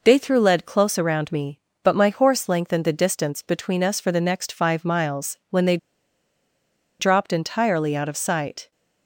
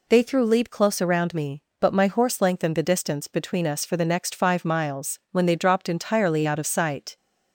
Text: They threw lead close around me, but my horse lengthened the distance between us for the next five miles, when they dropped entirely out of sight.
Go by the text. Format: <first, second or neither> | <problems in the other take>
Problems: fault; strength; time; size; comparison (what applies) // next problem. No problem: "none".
second | pauses between "they" and "dropped"; at 5.7 s; 1.2 s long